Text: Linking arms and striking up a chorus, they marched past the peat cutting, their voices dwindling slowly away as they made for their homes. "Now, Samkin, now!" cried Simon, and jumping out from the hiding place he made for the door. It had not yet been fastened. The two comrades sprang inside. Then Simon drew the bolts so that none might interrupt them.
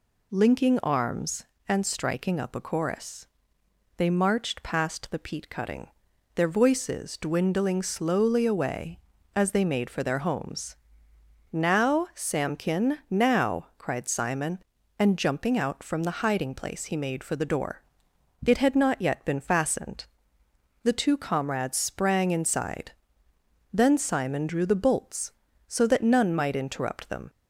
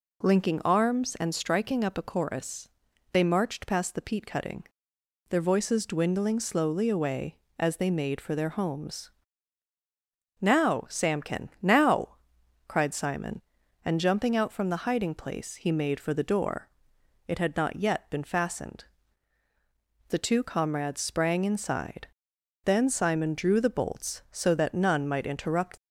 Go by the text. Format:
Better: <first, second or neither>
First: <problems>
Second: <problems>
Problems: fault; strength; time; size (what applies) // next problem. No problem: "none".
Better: first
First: none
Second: stops before "them"; at 25.7 s